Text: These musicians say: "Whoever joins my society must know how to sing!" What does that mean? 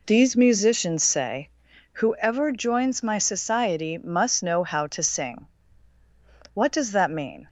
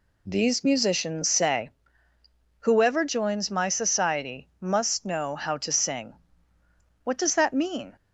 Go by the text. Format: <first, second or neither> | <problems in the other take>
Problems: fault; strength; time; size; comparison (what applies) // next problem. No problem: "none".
neither | none